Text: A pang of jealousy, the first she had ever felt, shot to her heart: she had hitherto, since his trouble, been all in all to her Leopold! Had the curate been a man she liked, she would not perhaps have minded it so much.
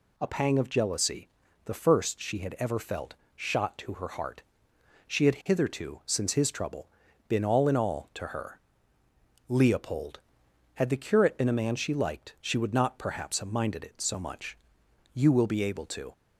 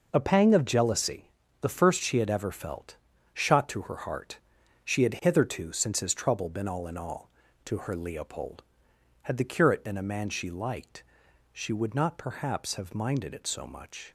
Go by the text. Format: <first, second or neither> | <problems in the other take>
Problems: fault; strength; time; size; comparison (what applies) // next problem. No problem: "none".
second | pauses between "her" and "Leopold"; noticeable; at 8.6 s; 0.88 s long // goes on to say "You will be able to"; noticeable; from 15.1 s on; 0.98 s long